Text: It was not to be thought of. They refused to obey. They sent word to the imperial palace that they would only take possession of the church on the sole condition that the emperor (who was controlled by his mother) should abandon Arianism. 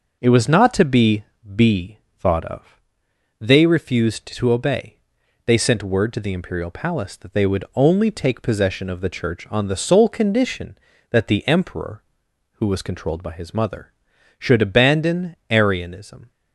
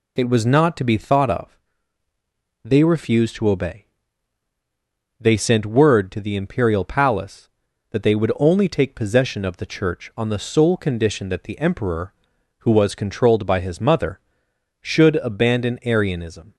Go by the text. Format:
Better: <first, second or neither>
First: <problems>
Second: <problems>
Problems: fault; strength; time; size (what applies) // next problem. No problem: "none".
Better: second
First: says "be" twice; at 1.5 s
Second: none